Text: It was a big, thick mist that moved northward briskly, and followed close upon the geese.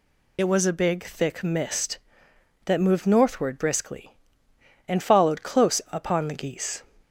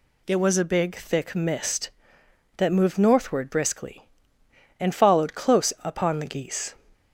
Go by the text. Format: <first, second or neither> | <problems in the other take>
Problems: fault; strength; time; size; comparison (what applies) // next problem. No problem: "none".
second | loses the start of "It"; at 0.3 s; 50 ms